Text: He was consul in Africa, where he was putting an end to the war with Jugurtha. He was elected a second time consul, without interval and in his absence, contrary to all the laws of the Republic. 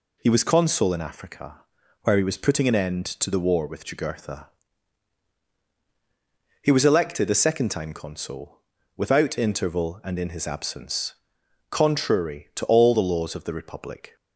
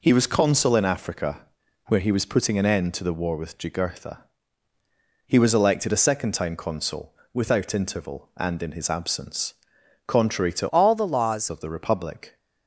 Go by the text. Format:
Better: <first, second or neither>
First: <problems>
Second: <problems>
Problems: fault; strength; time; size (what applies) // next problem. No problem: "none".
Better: first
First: none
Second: changes voice from "all" to "laws"; from 10.6 to 11.4 s; 0.8 s long